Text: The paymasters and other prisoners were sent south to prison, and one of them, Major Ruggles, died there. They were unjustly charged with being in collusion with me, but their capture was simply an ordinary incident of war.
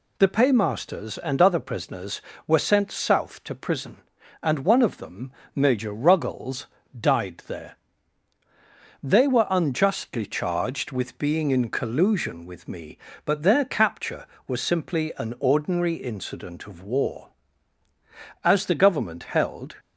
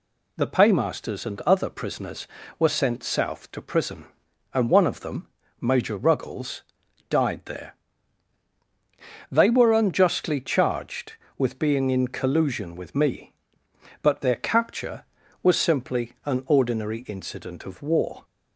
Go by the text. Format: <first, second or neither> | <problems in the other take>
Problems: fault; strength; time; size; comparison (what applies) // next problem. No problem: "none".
second | goes on to say "As the Government held"; from 18.4 s on; 1.3 s long